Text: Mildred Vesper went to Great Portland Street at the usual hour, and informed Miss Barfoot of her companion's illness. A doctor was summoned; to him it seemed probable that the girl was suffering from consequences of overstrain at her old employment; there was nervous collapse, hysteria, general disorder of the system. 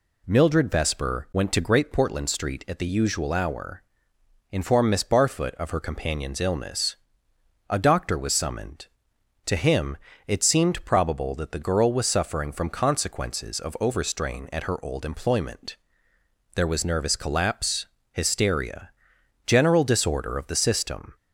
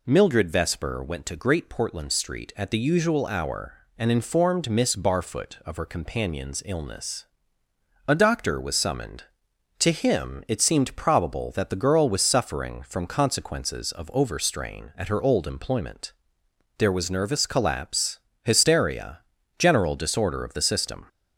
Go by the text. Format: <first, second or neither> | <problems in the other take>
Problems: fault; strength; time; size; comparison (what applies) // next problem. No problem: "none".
second | skips "and"; at 4.1 s // pauses between "him" and "it"; slight; at 9.9 s; 0.28 s long